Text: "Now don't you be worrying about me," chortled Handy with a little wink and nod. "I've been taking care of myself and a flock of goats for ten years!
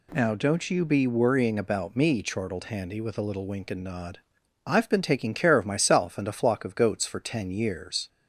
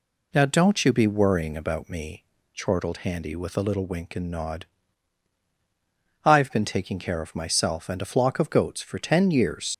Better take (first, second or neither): first